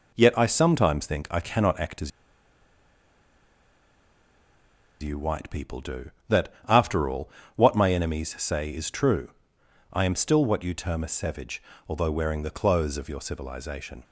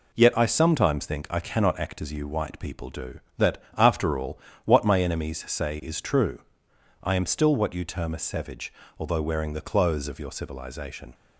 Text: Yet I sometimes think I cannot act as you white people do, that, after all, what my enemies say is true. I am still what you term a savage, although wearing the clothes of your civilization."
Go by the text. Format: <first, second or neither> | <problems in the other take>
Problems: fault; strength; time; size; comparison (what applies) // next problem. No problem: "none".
second | pauses between "as" and "you"; strong; at 2.1 s; 2.9 s long